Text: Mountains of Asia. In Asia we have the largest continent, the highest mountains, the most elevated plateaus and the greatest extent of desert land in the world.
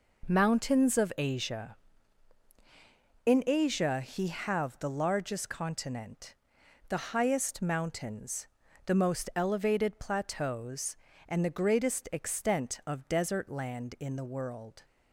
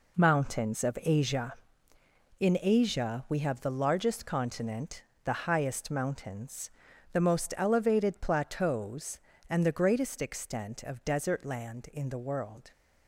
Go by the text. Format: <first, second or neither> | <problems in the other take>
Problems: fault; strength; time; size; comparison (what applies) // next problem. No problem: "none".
second | says "he" for "we"; at 4.0 s